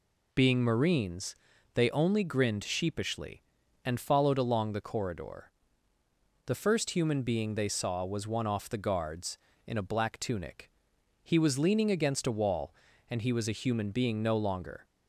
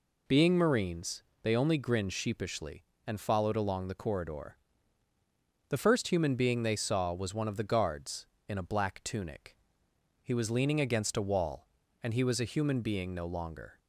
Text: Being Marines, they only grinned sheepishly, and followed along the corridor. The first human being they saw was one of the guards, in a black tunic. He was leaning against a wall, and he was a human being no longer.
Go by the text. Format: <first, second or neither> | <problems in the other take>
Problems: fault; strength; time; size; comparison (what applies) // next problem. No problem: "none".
second | says "off" for "of"; at 8.4 s